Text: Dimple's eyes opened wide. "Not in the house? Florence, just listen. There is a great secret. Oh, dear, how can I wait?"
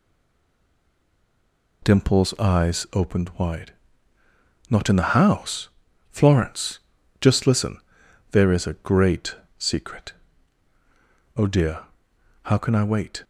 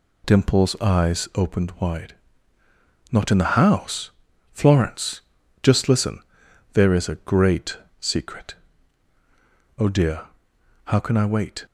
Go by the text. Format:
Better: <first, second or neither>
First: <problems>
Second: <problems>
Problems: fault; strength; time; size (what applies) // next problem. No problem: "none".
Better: second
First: stays silent before the first word; noticeable; until 1.8 s; 1.8 s long // pauses between "great" and "secret"; slight; at 9.3 s; 0.22 s long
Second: pauses between "great" and "secret"; slight; at 7.7 s; 0.22 s long